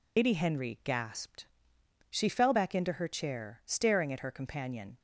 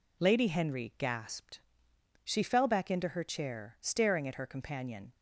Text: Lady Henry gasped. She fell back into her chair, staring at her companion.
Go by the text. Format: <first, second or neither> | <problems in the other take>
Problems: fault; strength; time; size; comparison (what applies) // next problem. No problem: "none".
second | loses the start of "Lady"; at 0.1 s; 110 ms